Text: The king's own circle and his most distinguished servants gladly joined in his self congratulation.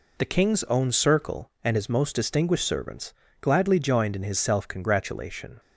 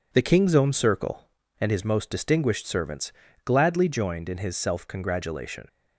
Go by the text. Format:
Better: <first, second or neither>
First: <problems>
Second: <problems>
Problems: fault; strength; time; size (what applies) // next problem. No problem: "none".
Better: neither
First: pauses between "servants" and "gladly"; slight; at 3.1 s; 0.26 s long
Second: pauses between "servants" and "gladly"; slight; at 3.1 s; 0.34 s long